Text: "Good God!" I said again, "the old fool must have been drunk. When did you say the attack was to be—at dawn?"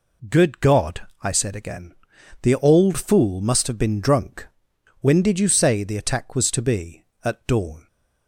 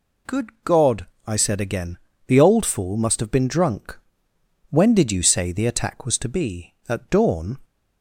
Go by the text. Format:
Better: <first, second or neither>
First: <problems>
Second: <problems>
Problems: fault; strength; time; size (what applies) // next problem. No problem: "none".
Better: neither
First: none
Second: none